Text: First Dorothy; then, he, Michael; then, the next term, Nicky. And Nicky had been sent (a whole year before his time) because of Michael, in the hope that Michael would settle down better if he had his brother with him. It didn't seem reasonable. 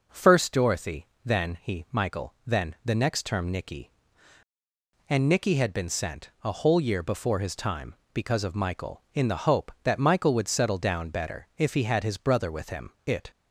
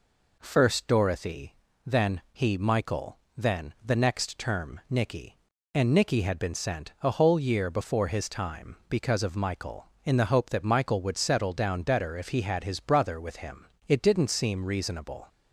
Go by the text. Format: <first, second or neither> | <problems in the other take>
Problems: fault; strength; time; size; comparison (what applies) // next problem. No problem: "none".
second | stops before "didn't seem reasonable"; at 13.3 s